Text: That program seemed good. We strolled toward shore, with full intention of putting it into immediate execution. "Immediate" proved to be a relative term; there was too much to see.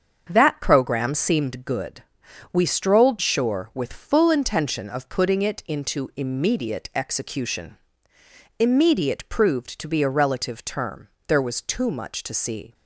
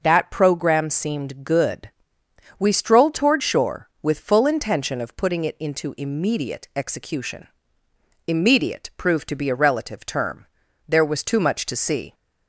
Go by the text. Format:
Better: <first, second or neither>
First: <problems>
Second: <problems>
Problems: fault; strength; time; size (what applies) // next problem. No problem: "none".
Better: second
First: starts louder than the rest; until 1.3 s; 7 dB // skips "toward"; at 3.1 s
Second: none